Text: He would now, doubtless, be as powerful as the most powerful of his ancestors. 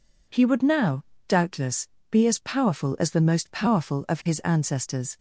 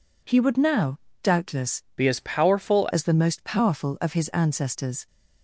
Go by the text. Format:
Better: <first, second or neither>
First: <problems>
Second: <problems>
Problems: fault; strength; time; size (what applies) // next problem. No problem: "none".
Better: first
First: none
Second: changes voice from "be" to "powerful"; from 1.9 to 2.8 s; 0.9 s long